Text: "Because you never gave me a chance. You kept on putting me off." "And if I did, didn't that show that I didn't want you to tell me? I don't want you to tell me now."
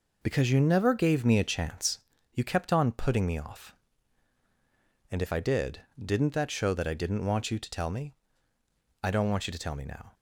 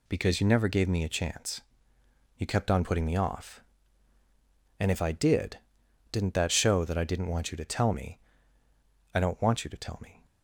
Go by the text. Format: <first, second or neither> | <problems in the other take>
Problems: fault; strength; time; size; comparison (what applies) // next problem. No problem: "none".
first | stops before "now"; at 10.2 s